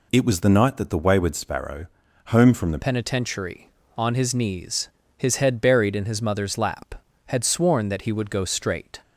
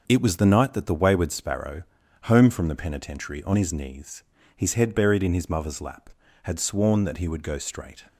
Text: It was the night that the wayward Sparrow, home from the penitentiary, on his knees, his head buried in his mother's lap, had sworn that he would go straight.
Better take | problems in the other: second | changes voice at "penitentiary"; from 2.8 s on; 6.1 s long

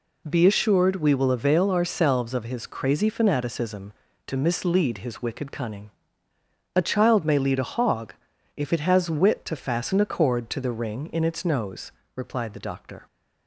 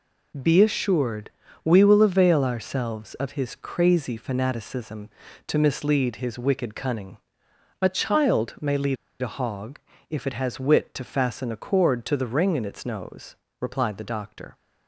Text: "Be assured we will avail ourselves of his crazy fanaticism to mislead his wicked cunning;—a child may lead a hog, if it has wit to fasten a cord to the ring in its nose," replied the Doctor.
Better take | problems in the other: first | pauses between "assured" and "we"; slight; at 1.2 s; 0.36 s long // pauses between "lead" and "a"; slight; at 8.9 s; 0.26 s long

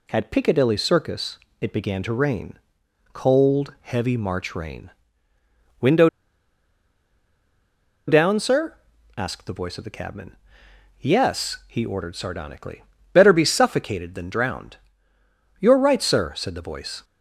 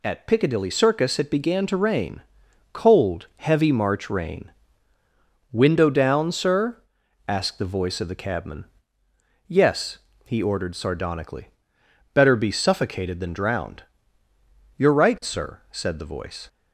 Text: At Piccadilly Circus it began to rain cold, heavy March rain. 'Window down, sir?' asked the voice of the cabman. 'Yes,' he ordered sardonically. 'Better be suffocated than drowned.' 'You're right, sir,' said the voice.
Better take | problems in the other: second | pauses between "Circus" and "it"; slight; at 1.3 s; 0.22 s long // pauses between "rain" and "cold"; noticeable; at 2.5 s; 0.56 s long; noticeable in the second // pauses between "Window" and "down"; strong; at 6.0 s; 1.9 s long

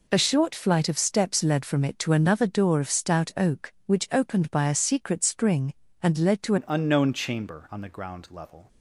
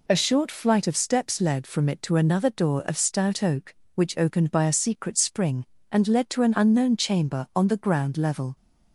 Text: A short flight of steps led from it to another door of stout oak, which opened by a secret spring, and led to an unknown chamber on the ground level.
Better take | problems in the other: second | changes voice at "an"; from 6.5 s on; 2.1 s long

